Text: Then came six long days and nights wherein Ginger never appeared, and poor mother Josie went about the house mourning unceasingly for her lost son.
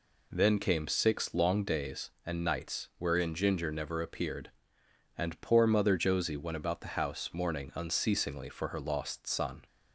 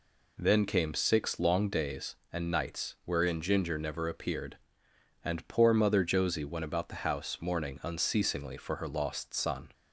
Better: neither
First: none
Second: none

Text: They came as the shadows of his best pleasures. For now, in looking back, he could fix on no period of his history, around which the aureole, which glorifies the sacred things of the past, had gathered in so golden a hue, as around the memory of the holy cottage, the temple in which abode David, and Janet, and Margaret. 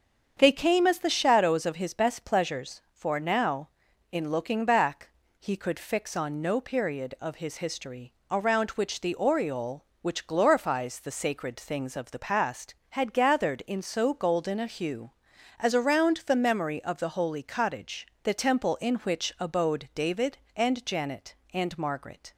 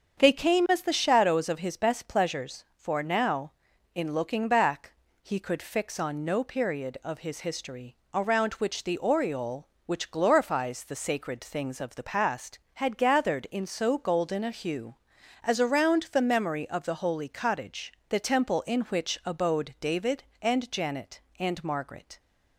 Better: neither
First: starts louder than the rest; strong; until 1.3 s; 7 dB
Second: starts louder than the rest; strong; until 1.2 s; 7 dB

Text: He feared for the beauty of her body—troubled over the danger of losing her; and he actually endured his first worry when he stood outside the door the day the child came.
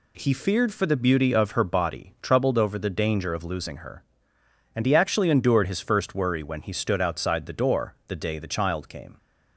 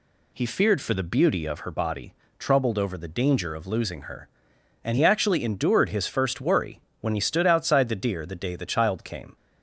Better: first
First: none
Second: pauses between "worry" and "when"; slight; at 6.7 s; 0.22 s long // says "deer" for "door"; at 7.9 s

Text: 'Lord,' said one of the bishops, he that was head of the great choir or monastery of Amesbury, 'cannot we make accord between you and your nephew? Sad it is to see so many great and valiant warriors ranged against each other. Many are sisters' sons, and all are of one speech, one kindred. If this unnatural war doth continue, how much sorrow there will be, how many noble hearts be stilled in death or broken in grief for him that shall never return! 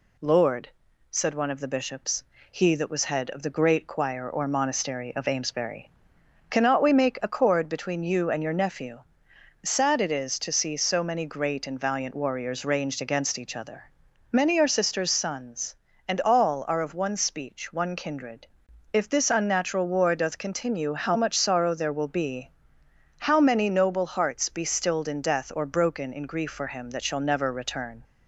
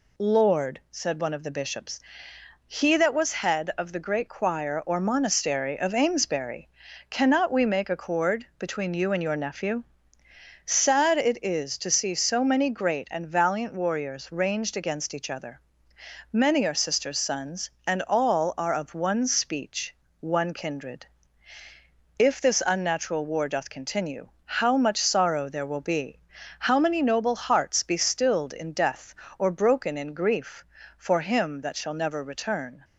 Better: neither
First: none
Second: none

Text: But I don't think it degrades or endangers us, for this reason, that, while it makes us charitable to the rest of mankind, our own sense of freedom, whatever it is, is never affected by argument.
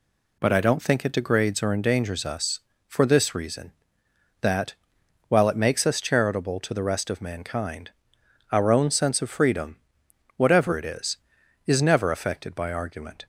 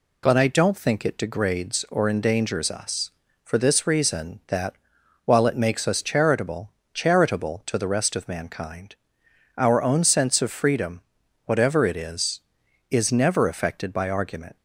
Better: first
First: none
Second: says "charitable" twice; at 6.9 s

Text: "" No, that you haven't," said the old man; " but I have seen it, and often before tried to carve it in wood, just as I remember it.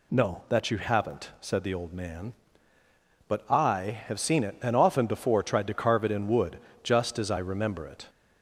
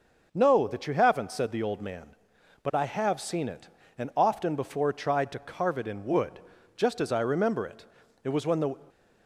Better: first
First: none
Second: goes on to say "It was when the"; from 8.2 s on; 0.52 s long

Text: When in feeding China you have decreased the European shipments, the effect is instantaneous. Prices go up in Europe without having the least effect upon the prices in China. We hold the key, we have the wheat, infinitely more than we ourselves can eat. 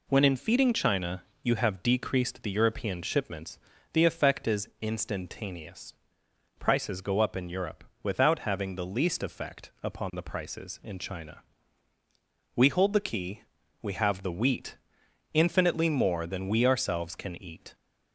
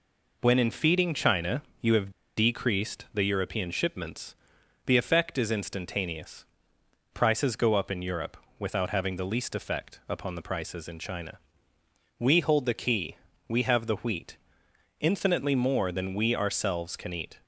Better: first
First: pauses between "China" and "you"; slight; at 1.2 s; 0.20 s long // pauses between "Europe" and "without"; slight; at 7.8 s; 0.18 s long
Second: pauses between "China" and "you"; slight; at 1.6 s; 0.18 s long // pauses between "have" and "decreased"; slight; at 2.1 s; 0.24 s long // pauses between "Europe" and "without"; slight; at 8.3 s; 0.22 s long

